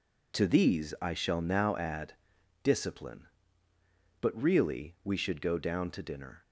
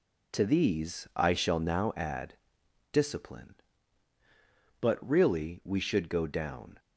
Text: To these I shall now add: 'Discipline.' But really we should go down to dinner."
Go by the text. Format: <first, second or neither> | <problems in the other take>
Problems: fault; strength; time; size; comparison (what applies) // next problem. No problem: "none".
first | stops before "to dinner"; at 6.7 s